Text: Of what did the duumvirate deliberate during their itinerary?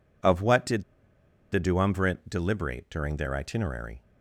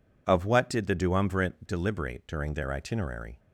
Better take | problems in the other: second | pauses between "did" and "the"; noticeable; at 0.8 s; 0.70 s long

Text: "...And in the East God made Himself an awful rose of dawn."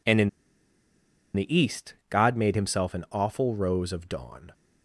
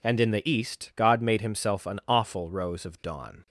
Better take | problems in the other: second | pauses between "in" and "the"; at 0.2 s; 1.0 s long // pauses between "East" and "God"; slight; at 1.9 s; 0.16 s long

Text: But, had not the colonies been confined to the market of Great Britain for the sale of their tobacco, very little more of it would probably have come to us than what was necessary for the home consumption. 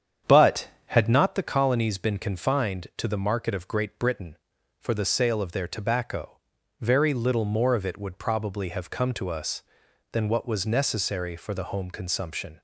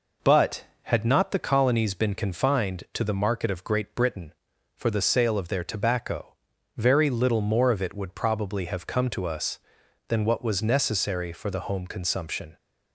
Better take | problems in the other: second | starts louder than the rest; strong; until 1.3 s; 8.5 dB

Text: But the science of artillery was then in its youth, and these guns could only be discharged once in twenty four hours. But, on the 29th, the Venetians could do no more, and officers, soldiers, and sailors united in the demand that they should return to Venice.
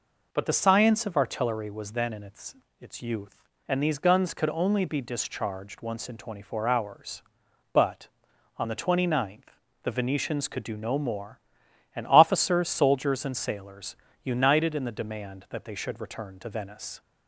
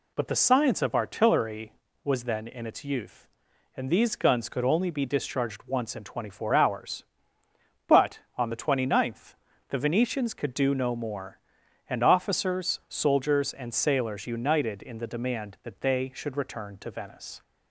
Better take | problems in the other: second | says "its" twice; at 2.7 s // pauses between "sailors" and "united"; slight; at 13.9 s; 0.26 s long

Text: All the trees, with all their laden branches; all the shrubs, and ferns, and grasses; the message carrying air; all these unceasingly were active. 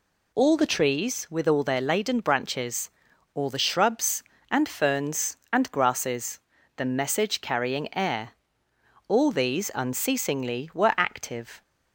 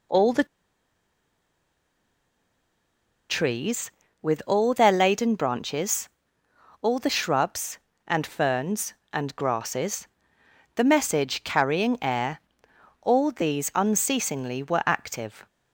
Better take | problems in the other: first | pauses between "the" and "trees"; strong; at 0.4 s; 2.8 s long

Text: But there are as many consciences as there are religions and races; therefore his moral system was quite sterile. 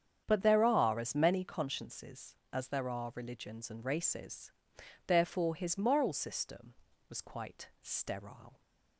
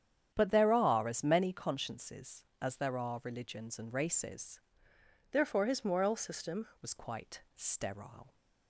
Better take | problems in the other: first | starts louder than the rest; strong; until 1.3 s; 9 dB; strong in the first // changes voice from "therefore" to "system"; from 5.3 to 6.6 s; 1.3 s long

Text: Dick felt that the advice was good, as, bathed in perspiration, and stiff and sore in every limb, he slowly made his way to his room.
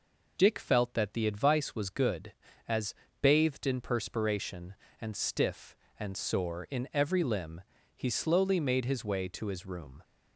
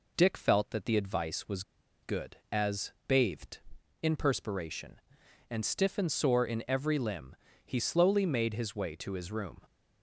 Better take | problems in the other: first | pauses between "was" and "good"; at 1.6 s; 0.39 s long

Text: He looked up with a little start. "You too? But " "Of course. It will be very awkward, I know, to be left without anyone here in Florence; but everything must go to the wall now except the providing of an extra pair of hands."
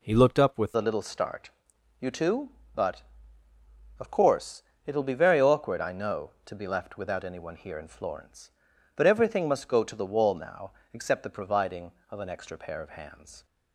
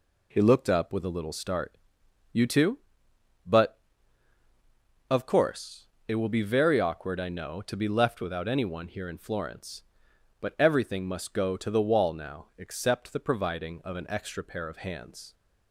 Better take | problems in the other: second | changes voice at "a"; from 0.7 s on; 12.7 s long // pauses between "now" and "except"; slight; at 10.7 s; 0.22 s long

